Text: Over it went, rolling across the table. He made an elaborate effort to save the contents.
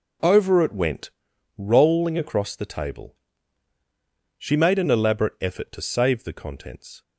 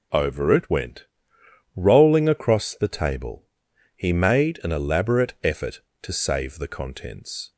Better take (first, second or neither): second